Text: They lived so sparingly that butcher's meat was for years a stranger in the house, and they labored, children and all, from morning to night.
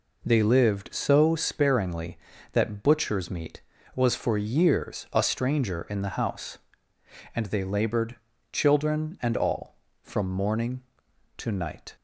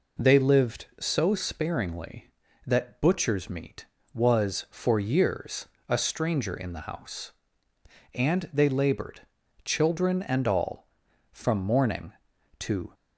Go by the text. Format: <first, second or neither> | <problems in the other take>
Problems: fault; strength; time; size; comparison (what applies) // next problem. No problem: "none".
first | pauses between "years" and "a"; slight; at 5.6 s; 0.20 s long // stops before "night"; at 12.9 s